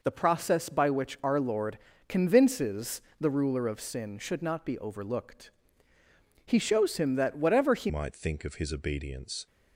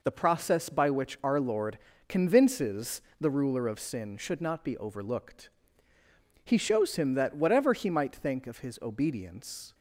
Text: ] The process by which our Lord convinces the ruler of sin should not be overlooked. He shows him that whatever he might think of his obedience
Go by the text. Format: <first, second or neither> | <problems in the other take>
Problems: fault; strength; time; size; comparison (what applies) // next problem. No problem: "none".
second | pauses between "Lord" and "convinces"; slight; at 1.7 s; 0.30 s long; slight in the second // pauses between "convinces" and "the"; slight; at 3.0 s; 0.18 s long; slight in the second // changes voice at "might"; from 7.8 s on; 1.6 s long